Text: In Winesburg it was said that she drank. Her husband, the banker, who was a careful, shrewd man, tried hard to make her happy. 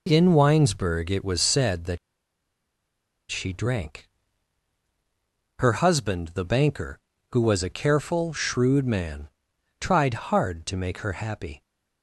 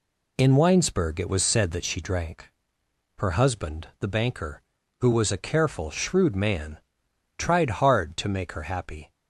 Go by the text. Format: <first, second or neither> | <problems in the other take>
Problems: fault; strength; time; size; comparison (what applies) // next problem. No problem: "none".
second | pauses between "that" and "she"; strong; at 1.9 s; 1.3 s long